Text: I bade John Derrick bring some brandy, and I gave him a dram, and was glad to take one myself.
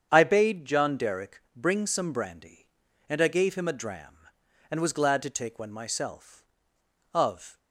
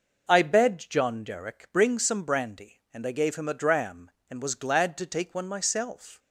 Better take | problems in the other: second | starts louder than the rest; strong; until 1.1 s; 7.5 dB // pauses between "Derrick" and "bring"; slight; at 1.4 s; 0.16 s long // goes on to say "Of"; slight; from 7.1 s on; 0.46 s long

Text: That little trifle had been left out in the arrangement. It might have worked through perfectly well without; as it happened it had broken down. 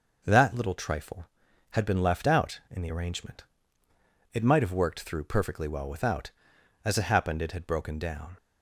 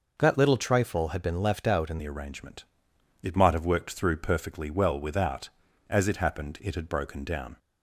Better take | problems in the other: first | changes voice at "the"; from 1.9 s on; 5.6 s long

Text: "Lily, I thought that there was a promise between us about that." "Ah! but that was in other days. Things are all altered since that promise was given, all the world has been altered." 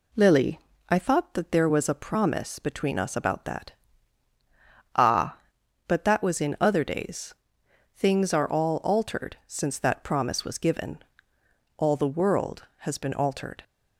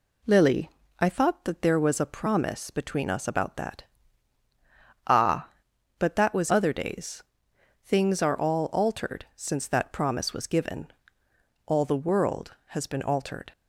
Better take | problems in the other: first | skips "in"; at 6.5 s

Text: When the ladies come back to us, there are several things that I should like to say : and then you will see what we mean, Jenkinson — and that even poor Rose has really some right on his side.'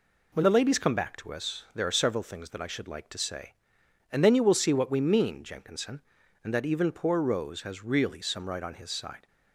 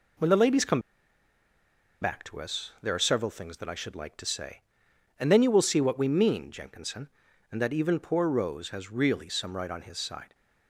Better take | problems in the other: first | pauses between "come" and "back"; at 0.8 s; 1.2 s long

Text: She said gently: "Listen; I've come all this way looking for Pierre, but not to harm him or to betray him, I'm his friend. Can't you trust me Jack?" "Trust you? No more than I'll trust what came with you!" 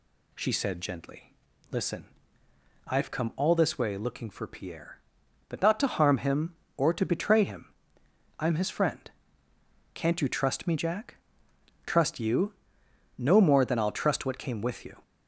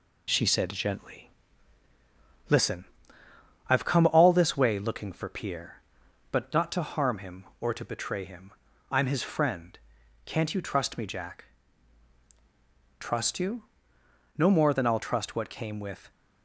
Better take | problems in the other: first | stops before "you"; at 16.1 s

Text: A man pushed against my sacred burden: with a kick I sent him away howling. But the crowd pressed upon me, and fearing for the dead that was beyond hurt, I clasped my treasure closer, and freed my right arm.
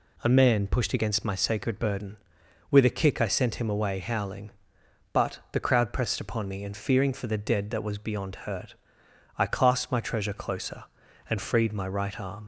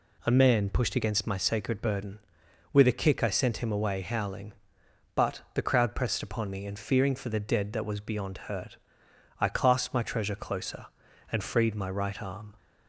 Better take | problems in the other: second | leaves "arm" unfinished; at 12.4 s; 70 ms

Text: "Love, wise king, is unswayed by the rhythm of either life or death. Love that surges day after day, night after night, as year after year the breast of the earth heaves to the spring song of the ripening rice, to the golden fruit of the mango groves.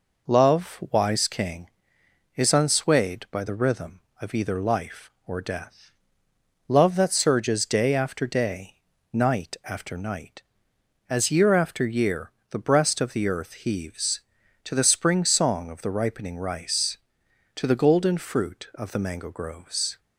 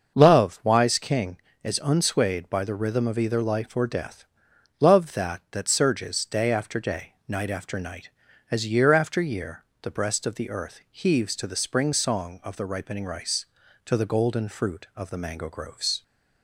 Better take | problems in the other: first | starts louder than the rest; until 1.2 s; 6.5 dB // says "that" twice; at 5.5 s // pauses between "year" and "the"; slight; at 9.6 s; 0.18 s long; slight in the first

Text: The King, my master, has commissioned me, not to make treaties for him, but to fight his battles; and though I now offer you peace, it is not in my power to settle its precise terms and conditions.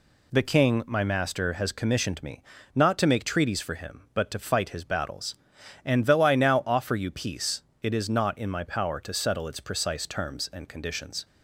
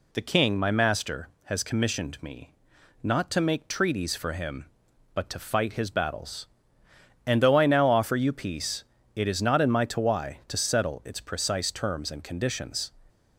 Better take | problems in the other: first | says "tawai" for "power"; at 9.8 s

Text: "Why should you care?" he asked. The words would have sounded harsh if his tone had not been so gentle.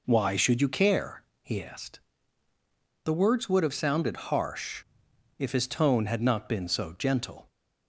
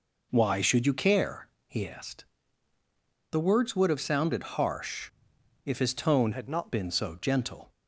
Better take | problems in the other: first | pauses between "harsh" and "if"; noticeable; at 5.1 s; 0.54 s long; noticeable in the first // changes voice from "had" to "not"; from 6.3 to 6.7 s; 0.4 s long

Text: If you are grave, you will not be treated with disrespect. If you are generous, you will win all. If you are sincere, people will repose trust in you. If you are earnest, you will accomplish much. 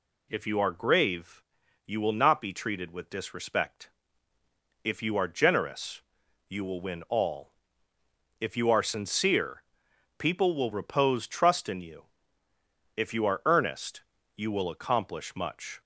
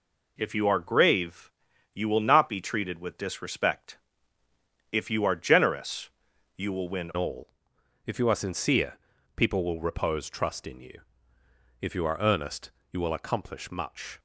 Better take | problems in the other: first | changes voice at "all"; from 7.1 s on; 7.0 s long

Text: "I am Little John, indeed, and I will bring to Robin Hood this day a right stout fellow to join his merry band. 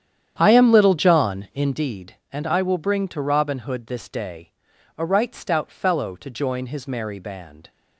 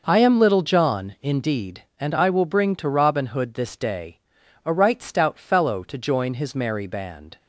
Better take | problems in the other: second | starts louder than the rest; strong; until 1.8 s; 9.5 dB // pauses between "day" and "a"; at 4.5 s; 0.44 s long; also in the second

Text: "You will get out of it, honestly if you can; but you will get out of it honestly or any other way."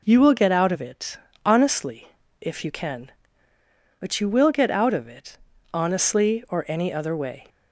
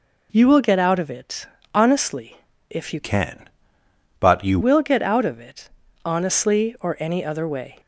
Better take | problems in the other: first | pauses between "honestly" and "if"; slight; at 2.3 s; 0.32 s long; slight in the first // changes voice from "can" to "you"; from 3.0 to 4.5 s; 1.5 s long // pauses between "it" and "honestly"; at 5.6 s; 0.38 s long; also in the first

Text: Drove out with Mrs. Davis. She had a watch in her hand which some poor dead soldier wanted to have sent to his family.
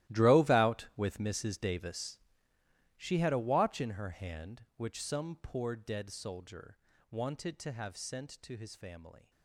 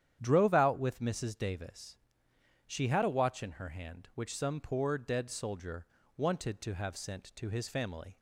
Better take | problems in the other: second | gets quieter; strong; throughout; 16.5 dB // starts louder than the rest; strong; until 1.2 s; 15 dB; strong in the second // pauses between "soldier" and "wanted"; slight; at 6.7 s; 0.34 s long; slight in the second

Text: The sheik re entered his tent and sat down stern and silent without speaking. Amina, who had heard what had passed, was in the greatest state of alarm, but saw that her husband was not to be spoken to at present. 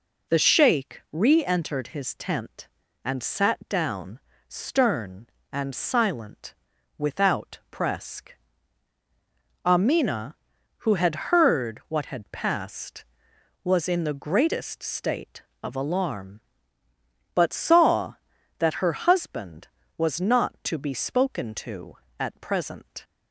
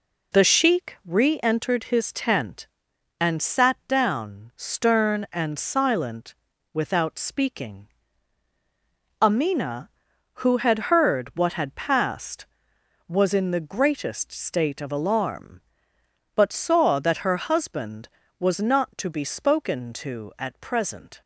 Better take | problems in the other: second | pauses between "down" and "stern"; slight; at 4.1 s; 0.28 s long // pauses between "silent" and "without"; at 6.5 s; 0.42 s long; also in the second // says "presque" for "speaking"; at 7.6 s

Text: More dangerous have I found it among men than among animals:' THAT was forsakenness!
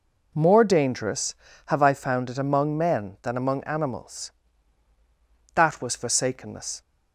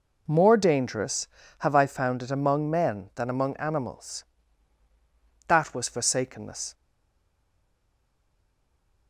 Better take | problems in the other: first | stays silent after the last word; from 6.7 s on; 2.3 s long

